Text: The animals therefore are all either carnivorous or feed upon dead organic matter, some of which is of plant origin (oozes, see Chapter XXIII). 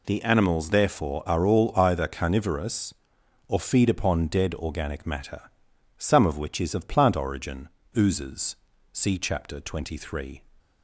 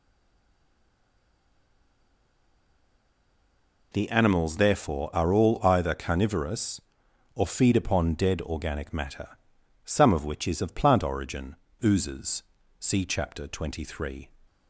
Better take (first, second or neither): first